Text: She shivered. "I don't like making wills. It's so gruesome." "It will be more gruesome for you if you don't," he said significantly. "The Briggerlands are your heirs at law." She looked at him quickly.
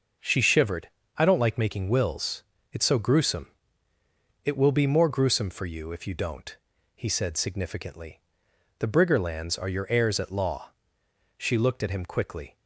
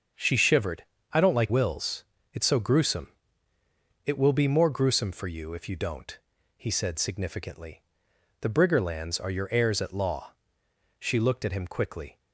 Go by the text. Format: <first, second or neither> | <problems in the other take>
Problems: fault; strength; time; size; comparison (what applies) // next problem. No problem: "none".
first | starts louder than the rest; until 1.4 s; 6.5 dB; noticeable in the first // skips "making"; at 1.4 s